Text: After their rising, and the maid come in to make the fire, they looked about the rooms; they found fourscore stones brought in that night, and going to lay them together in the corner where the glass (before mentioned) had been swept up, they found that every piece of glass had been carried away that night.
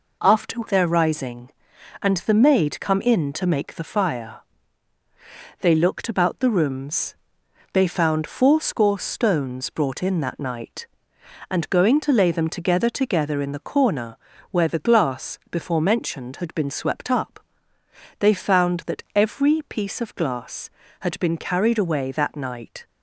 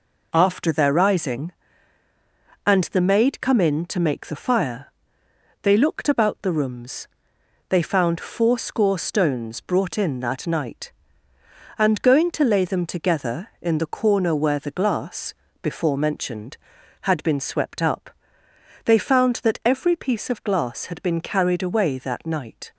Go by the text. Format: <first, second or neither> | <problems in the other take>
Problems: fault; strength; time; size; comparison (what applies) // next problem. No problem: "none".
second | says "together" twice; at 12.8 s // pauses between "corner" and "where"; slight; at 14.1 s; 0.32 s long